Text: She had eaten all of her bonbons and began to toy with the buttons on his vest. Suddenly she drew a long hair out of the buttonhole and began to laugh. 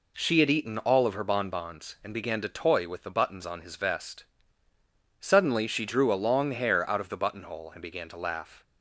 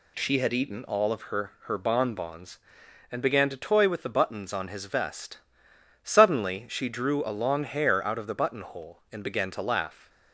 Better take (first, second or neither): first